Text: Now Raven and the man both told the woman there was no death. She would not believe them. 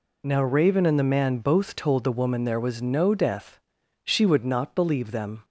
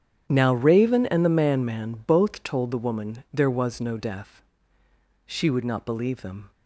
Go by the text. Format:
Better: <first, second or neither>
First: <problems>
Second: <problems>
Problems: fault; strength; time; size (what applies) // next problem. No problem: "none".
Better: first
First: none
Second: starts louder than the rest; strong; until 1.3 s; 9.5 dB // says "man" twice; at 1.6 s